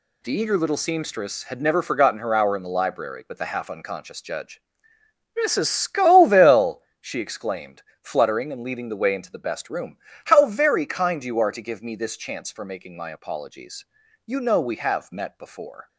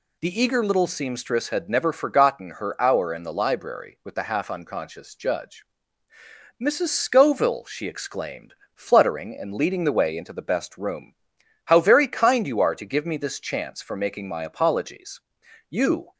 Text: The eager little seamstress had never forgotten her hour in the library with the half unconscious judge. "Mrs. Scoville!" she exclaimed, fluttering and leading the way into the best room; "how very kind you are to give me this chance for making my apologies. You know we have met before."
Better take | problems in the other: first | stops before "know we have met before"; at 16.1 s

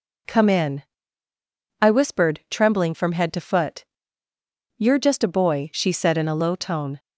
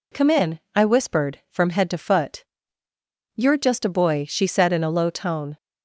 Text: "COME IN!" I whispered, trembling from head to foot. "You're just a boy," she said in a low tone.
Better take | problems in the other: first | skips "trembling"; at 1.4 s

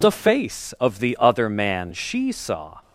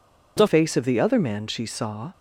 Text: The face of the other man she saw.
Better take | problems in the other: first | changes voice at "face"; from 0.4 s on; 1.7 s long

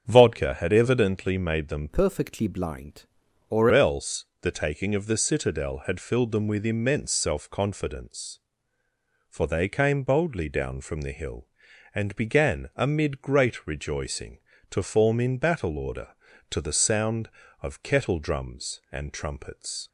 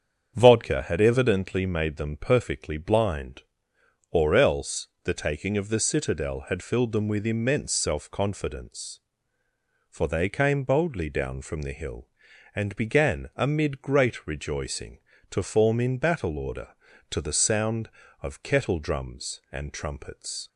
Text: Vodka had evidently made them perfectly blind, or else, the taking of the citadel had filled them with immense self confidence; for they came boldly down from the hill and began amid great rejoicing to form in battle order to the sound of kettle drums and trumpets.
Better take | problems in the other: second | starts louder than the rest; strong; until 1.0 s; 7.5 dB; strong in the second // changes voice from "perfectly" to "or"; from 1.8 to 3.6 s; 1.8 s long

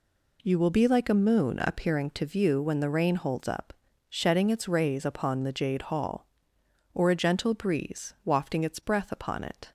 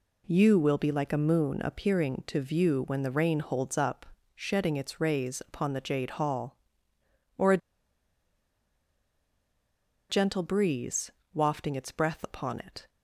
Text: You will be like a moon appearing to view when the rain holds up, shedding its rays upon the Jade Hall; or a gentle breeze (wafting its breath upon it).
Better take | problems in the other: first | pauses between "a" and "gentle"; strong; at 7.5 s; 2.5 s long

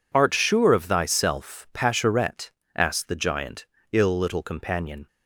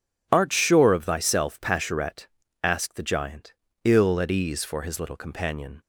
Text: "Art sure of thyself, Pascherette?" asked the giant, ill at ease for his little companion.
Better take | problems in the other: second | skips "at ease for his"; at 4.1 s

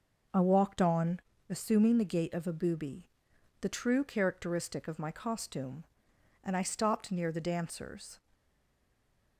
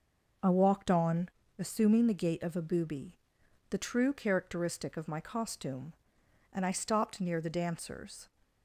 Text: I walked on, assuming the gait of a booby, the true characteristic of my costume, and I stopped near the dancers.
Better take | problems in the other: second | stays silent after the last word; from 8.3 s on; 1.0 s long

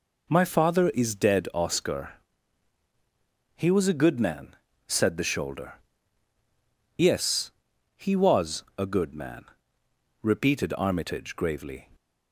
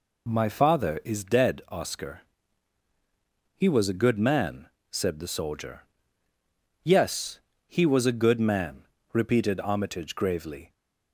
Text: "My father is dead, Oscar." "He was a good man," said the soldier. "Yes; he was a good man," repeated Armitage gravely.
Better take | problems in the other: second | says "shoulder" for "soldier"; at 5.2 s

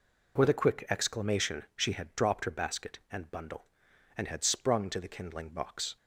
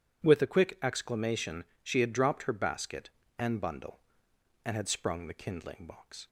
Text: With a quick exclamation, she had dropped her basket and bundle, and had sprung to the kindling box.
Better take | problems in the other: first | skips "to"; at 5.2 s

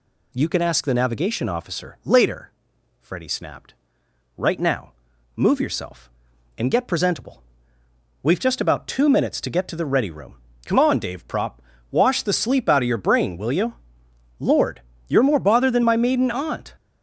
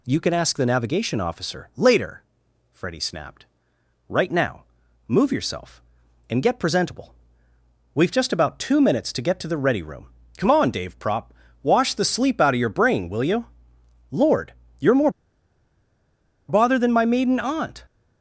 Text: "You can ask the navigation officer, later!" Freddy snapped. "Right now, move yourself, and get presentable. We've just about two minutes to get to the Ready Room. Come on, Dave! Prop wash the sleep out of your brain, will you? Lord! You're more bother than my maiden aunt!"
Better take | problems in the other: first | pauses between "Prop" and "wash"; slight; at 11.3 s; 0.30 s long; slight in the first // pauses between "more" and "bother"; strong; at 15.1 s; 1.3 s long

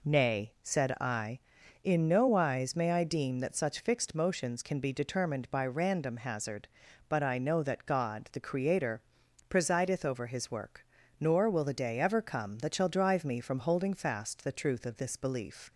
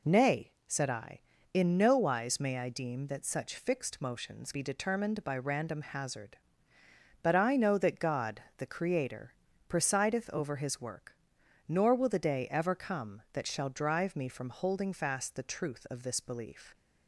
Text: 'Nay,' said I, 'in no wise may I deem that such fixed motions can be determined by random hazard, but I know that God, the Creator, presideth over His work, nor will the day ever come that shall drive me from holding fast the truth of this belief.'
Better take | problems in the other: first | skips "can"; at 4.5 s

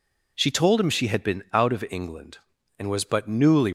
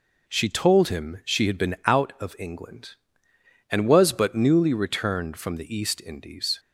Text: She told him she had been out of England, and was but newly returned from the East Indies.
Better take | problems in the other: second | stops before "returned from the East Indies"; at 3.6 s

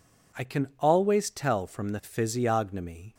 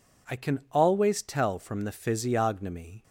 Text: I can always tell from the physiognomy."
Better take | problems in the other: neither | none

